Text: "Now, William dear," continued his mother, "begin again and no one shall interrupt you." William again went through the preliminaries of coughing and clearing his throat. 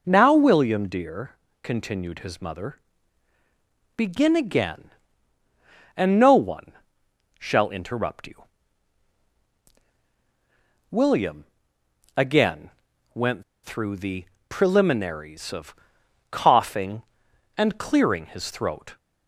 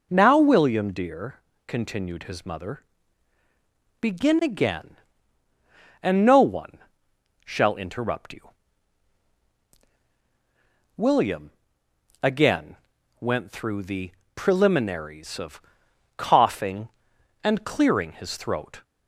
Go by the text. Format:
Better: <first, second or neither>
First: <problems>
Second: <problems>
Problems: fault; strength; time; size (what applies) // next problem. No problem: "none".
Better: second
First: pauses between "one" and "shall"; noticeable; at 6.7 s; 0.66 s long // pauses between "William" and "again"; noticeable; at 11.4 s; 0.72 s long // pauses between "again" and "went"; at 12.7 s; 0.42 s long // pauses between "went" and "through"; slight; at 13.4 s; 0.20 s long // pauses between "the" and "preliminaries"; slight; at 14.2 s; 0.24 s long // pauses between "of" and "coughing"; noticeable; at 15.7 s; 0.56 s long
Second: pauses between "one" and "shall"; noticeable; at 6.7 s; 0.66 s long // pauses between "William" and "again"; noticeable; at 11.5 s; 0.72 s long // pauses between "again" and "went"; at 12.7 s; 0.42 s long // pauses between "the" and "preliminaries"; slight; at 14.1 s; 0.24 s long // pauses between "of" and "coughing"; noticeable; at 15.6 s; 0.56 s long